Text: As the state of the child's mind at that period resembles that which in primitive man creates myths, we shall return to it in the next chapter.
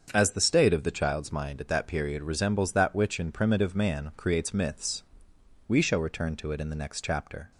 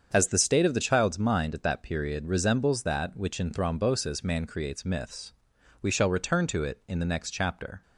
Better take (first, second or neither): first